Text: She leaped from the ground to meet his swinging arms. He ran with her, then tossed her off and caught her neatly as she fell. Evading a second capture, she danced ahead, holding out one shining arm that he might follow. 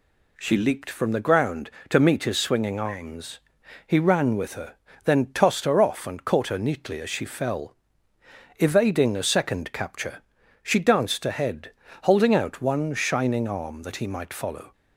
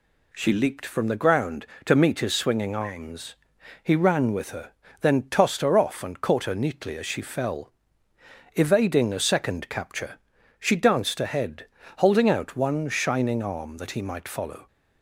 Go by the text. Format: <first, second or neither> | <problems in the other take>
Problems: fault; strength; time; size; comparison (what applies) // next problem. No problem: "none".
neither | none